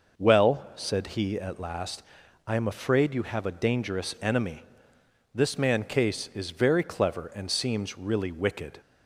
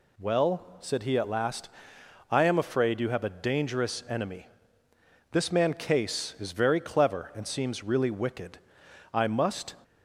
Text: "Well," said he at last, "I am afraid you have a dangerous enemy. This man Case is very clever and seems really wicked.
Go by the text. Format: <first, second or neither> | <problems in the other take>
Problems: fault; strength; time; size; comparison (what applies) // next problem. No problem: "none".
first | goes on to say "I must"; noticeable; from 9.1 s on; 0.64 s long